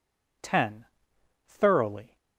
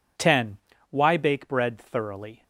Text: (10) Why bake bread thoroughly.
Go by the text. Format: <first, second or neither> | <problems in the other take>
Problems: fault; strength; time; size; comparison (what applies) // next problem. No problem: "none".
second | skips "Why bake bread"; at 1.1 s